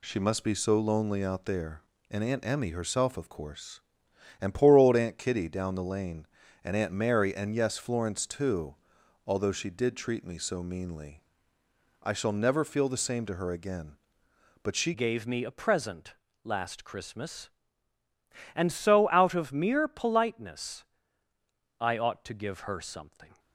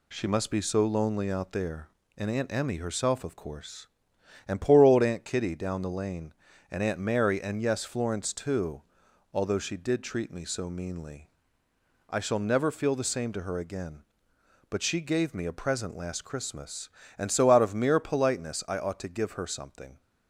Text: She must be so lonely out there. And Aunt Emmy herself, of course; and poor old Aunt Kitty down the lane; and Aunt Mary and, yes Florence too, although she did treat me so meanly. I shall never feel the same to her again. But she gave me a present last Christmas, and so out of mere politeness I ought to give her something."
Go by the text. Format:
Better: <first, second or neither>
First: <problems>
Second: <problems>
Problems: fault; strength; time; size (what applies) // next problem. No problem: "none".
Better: second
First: changes voice at "gave"; from 14.9 s on; 8.4 s long // pauses between "present" and "last"; slight; at 16.1 s; 0.28 s long // pauses between "politeness" and "I"; noticeable; at 20.8 s; 0.96 s long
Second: none